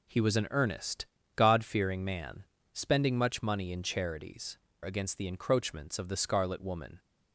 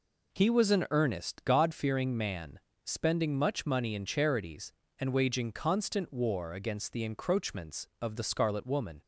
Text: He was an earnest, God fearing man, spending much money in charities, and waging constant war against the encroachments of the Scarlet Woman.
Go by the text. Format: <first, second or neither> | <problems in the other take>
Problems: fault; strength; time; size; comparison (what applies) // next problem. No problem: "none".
second | skips "and waging constant war"; at 4.7 s